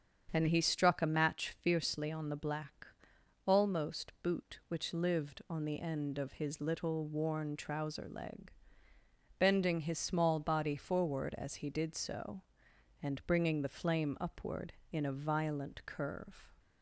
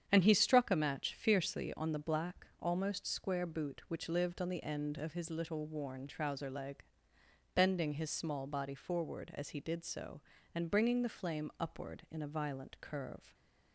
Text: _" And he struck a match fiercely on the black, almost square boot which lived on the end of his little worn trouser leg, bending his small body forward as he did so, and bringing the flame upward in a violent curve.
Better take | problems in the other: second | starts louder than the rest; strong; until 1.3 s; 7.5 dB; strong in the second // skips "square"; at 4.1 s

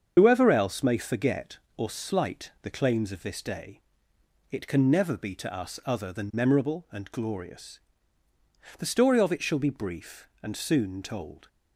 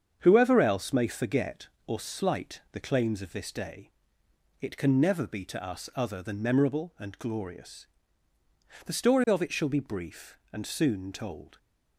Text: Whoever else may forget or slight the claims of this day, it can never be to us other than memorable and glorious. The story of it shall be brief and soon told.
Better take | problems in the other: second | loses the start of "Whoever"; at 0.1 s; 50 ms // starts louder than the rest; strong; until 1.1 s; 7.5 dB; strong in the second

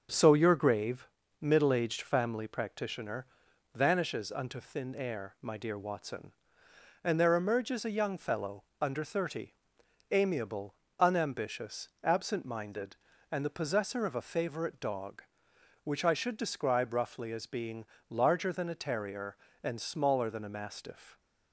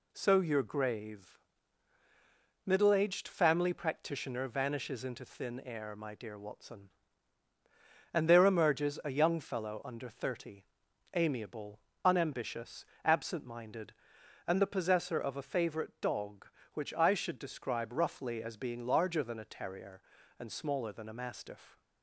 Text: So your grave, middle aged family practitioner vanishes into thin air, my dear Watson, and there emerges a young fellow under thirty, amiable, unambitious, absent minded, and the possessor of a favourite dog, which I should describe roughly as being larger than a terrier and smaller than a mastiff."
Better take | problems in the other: second | starts louder than the rest; until 1.4 s; 7 dB // pauses between "practitioner" and "vanishes"; noticeable; at 3.2 s; 0.50 s long // says "unto" for "into"; at 4.3 s // pauses between "fellow" and "under"; slight; at 8.6 s; 0.18 s long // pauses between "being" and "larger"; slight; at 17.8 s; 0.26 s long

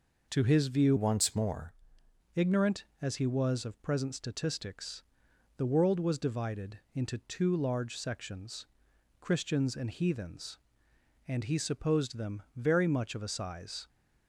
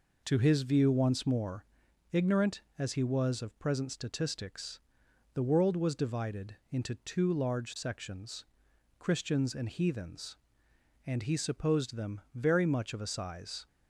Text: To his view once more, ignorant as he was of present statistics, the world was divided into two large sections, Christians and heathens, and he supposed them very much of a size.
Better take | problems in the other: second | changes voice from "once" to "more"; from 0.9 to 1.7 s; 0.8 s long // pauses between "divided" and "into"; slight; at 6.7 s; 0.16 s long; slight in the second

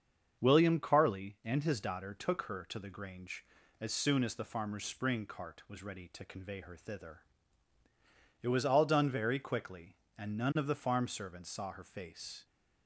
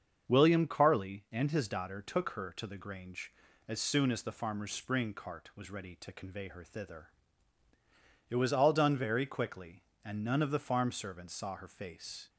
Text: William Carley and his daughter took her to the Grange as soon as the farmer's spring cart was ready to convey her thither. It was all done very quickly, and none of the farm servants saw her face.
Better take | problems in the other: neither | starts louder than the rest; the same in both

